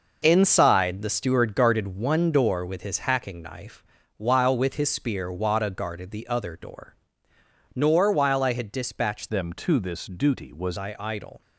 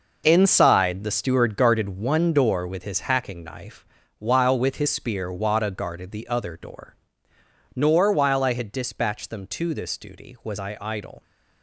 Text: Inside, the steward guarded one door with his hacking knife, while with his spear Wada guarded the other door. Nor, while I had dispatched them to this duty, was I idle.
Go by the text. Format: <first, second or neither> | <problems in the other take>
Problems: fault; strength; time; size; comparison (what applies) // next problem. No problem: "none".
second | changes voice from "them" to "was"; from 9.2 to 10.7 s; 1.5 s long